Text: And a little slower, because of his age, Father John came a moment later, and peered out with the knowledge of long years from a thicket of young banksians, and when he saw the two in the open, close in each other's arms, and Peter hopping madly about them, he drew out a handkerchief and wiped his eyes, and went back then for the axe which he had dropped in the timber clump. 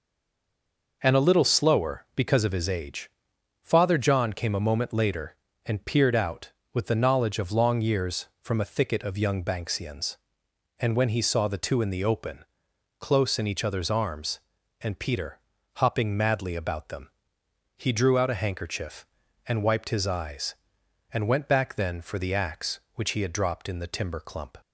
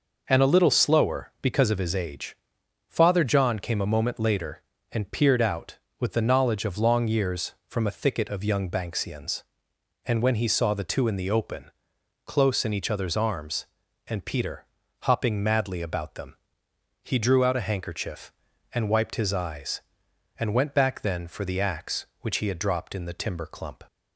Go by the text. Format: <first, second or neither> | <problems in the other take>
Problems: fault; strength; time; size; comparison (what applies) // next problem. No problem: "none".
second | stays silent before the first word; until 1.0 s; 1.0 s long // pauses between "Peter" and "hopping"; at 15.3 s; 0.38 s long; also in the second